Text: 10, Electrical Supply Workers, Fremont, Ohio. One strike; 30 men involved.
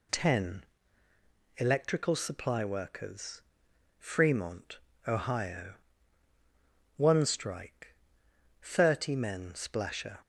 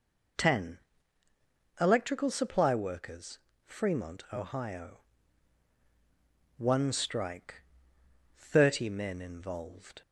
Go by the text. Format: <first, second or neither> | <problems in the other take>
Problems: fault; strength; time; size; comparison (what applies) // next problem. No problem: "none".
second | says "splasher" for "involved"; at 9.5 s